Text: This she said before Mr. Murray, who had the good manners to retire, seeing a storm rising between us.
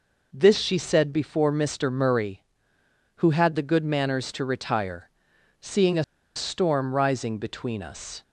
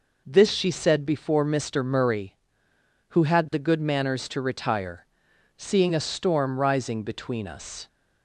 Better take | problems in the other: second | pauses between "a" and "storm"; slight; at 6.0 s; 0.32 s long

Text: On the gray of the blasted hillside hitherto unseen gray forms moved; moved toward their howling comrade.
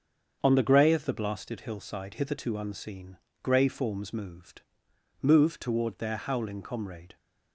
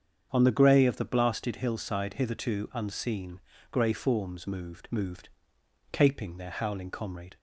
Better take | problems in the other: first | starts louder than the rest; strong; until 1.3 s; 7.5 dB; strong in the first // pauses between "unseen" and "gray"; slight; at 3.3 s; 0.32 s long; slight in the first // says "caping" for "toward"; at 5.9 s

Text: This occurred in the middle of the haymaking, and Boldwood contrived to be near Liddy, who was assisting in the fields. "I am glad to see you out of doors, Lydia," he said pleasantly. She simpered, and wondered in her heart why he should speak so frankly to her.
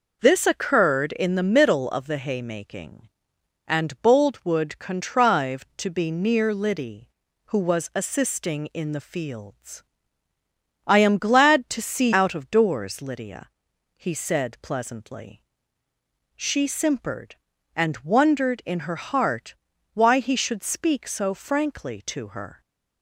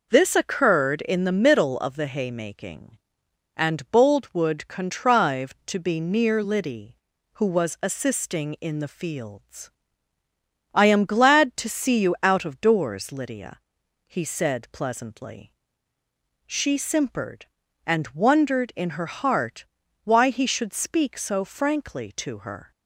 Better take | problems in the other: second | skips "you"; at 12.1 s // pauses between "heart" and "why"; at 19.5 s; 0.40 s long; also in the second

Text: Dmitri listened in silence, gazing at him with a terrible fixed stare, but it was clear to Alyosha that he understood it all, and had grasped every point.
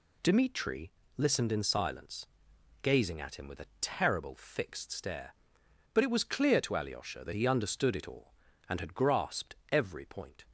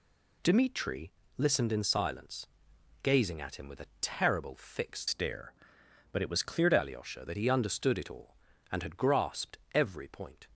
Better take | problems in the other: first | pauses between "Dmitri" and "listened"; slight; at 1.1 s; 0.26 s long; slight in the first // changes voice from "stare" to "to"; from 5.0 to 6.7 s; 1.7 s long // pauses between "grasped" and "every"; slight; at 9.5 s; 0.16 s long; slight in the first

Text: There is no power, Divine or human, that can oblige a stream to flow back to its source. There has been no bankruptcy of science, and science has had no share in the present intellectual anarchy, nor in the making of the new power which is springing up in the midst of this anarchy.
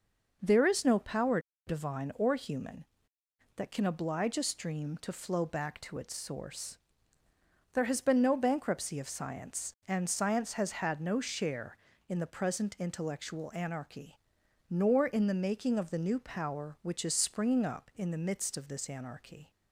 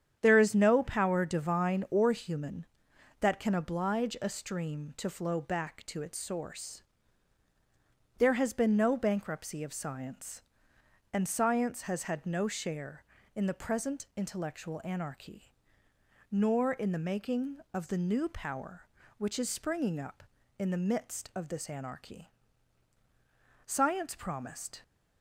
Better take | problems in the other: first | starts louder than the rest; strong; until 1.2 s; 9 dB // goes on to say "Science promised"; noticeable; from 23.6 s on; 1.1 s long

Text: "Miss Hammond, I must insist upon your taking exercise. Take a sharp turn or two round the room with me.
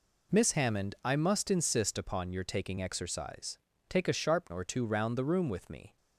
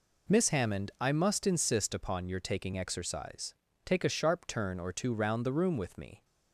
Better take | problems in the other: second | skips "turn"; at 4.5 s

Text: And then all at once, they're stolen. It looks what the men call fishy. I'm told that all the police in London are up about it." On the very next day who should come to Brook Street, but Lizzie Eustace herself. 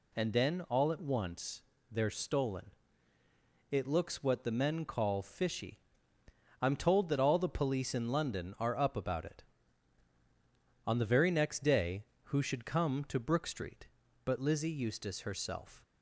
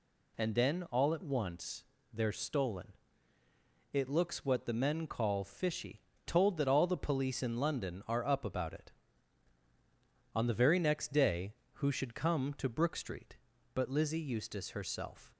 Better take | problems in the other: first | skips "I'm"; at 6.1 s

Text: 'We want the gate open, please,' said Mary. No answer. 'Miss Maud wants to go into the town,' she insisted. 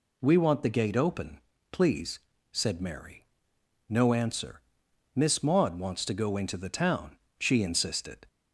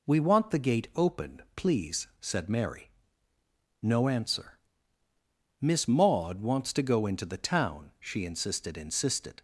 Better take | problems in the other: first | says "insisted" twice; at 8.7 s

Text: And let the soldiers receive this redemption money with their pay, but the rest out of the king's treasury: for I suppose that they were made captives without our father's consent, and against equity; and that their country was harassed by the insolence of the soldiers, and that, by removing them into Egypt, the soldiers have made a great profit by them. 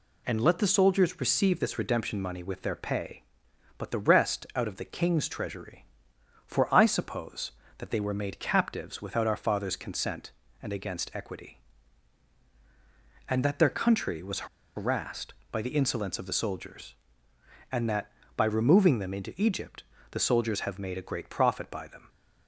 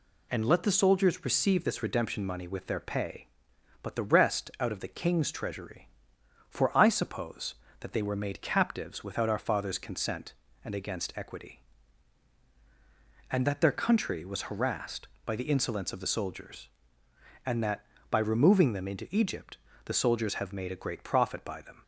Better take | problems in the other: second | pauses between "was" and "harassed"; slight; at 14.4 s; 0.28 s long

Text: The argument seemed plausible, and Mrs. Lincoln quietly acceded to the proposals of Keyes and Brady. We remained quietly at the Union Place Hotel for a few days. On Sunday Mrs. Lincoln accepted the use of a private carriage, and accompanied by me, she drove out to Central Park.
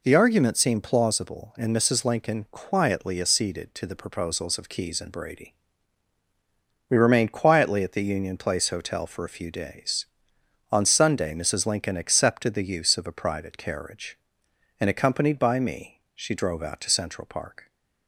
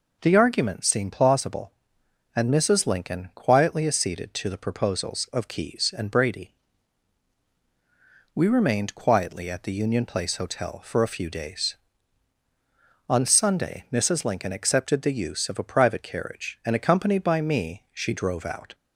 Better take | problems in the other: first | stops before "to Central Park"; at 18.7 s

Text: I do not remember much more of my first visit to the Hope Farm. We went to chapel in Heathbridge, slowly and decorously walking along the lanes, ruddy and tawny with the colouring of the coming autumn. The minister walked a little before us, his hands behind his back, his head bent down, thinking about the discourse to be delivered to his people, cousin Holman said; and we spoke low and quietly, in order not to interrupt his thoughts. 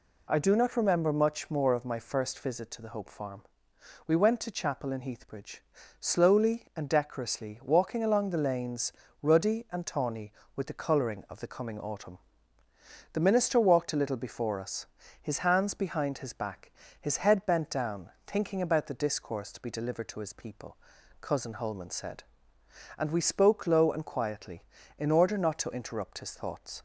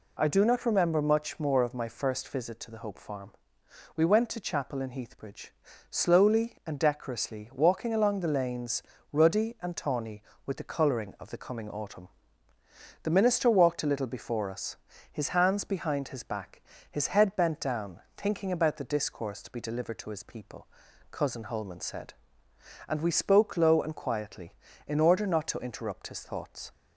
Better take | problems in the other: neither | none

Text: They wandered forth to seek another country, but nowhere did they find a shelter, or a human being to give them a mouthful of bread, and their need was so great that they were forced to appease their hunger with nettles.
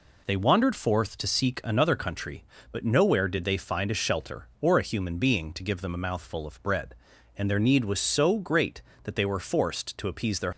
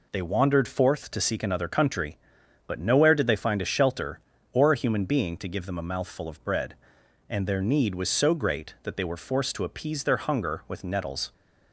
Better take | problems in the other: second | stops before "hunger with nettles"; at 10.5 s

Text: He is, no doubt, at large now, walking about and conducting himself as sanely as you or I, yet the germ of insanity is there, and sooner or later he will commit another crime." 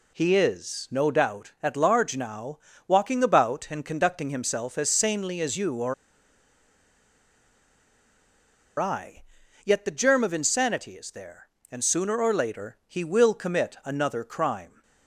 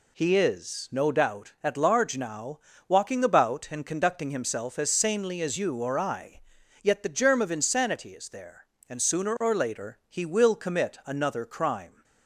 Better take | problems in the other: second | pauses between "or" and "I"; strong; at 5.9 s; 2.8 s long

